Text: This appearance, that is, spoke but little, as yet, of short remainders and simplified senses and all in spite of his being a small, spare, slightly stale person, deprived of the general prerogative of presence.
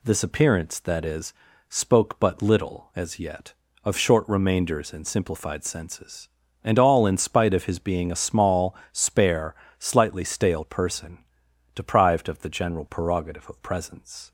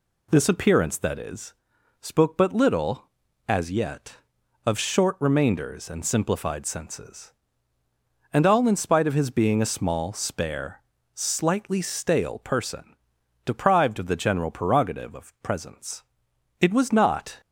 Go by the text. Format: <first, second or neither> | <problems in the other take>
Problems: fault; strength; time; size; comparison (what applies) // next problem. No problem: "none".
first | goes on to say "It was not"; noticeable; from 16.6 s on; 0.80 s long